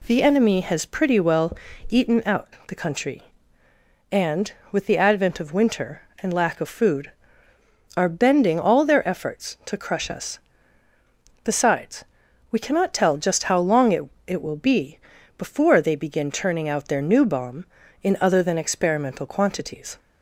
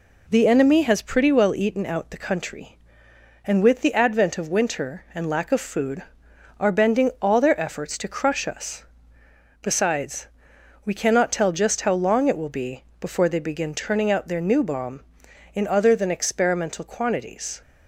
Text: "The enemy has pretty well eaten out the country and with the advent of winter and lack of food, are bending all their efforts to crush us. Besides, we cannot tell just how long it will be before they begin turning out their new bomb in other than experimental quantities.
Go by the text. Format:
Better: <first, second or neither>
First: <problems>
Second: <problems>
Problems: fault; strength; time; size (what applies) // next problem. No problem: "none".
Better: second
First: pauses between "well" and "eaten"; slight; at 1.5 s; 0.32 s long // pauses between "out" and "the"; slight; at 2.4 s; 0.18 s long // says "it" twice; at 14.2 s // pauses between "be" and "before"; at 14.9 s; 0.38 s long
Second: pauses between "be" and "before"; slight; at 12.8 s; 0.16 s long